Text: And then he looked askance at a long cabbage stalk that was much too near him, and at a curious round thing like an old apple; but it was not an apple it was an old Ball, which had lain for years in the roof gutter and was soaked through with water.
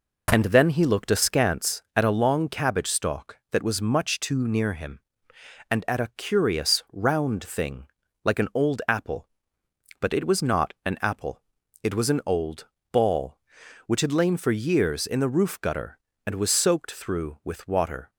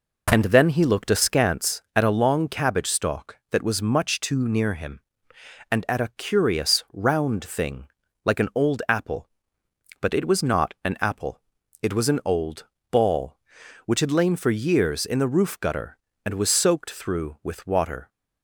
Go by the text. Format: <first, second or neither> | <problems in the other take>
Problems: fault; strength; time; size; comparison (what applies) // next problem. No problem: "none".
neither | pauses between "thing" and "like"; the same in both // pauses between "apple" and "it"; the same in both // pauses between "old" and "Ball"; slight; the same in both